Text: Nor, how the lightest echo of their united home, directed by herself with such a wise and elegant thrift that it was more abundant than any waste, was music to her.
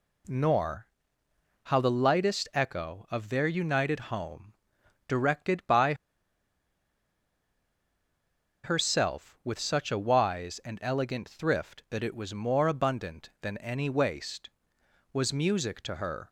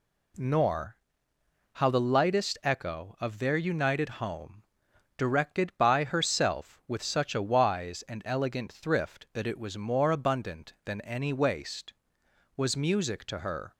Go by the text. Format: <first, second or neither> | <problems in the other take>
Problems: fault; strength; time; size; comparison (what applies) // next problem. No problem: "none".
second | pauses between "by" and "herself"; strong; at 5.9 s; 2.6 s long